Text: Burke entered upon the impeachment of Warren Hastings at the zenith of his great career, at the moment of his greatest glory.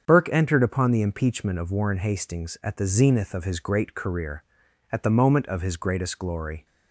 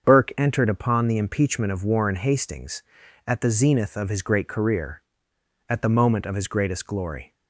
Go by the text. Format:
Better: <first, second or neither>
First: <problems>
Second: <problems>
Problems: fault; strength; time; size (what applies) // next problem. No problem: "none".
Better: neither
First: starts louder than the rest; strong; until 1.0 s; 7.5 dB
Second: starts louder than the rest; until 1.1 s; 7 dB